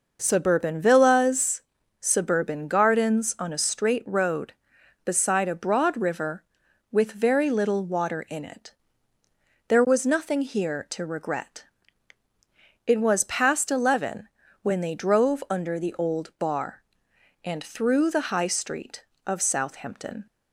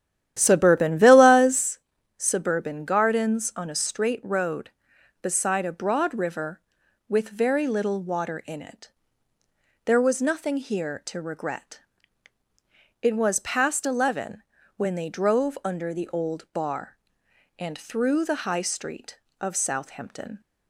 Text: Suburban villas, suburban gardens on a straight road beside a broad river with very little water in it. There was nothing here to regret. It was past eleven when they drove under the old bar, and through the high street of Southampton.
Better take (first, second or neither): first